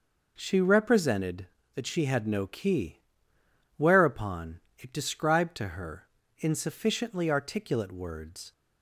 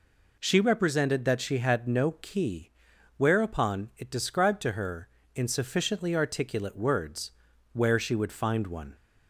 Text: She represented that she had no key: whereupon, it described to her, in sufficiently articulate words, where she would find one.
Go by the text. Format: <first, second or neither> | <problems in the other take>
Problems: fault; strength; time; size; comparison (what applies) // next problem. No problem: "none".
second | stops before "where she would find one"; at 8.5 s